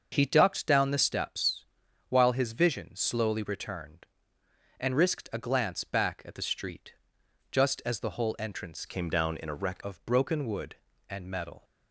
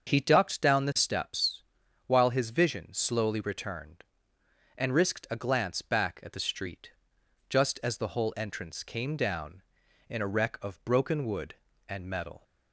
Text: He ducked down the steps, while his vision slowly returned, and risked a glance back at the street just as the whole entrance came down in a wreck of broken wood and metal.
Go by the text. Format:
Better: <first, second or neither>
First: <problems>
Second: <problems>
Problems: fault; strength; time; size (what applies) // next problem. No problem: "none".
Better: second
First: starts louder than the rest; until 1.1 s; 6.5 dB // pauses between "street" and "just"; noticeable; at 6.9 s; 0.58 s long // changes voice from "came" to "wreck"; from 8.8 to 9.8 s; 1.0 s long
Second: starts louder than the rest; until 1.1 s; 6.5 dB // pauses between "street" and "just"; noticeable; at 6.9 s; 0.58 s long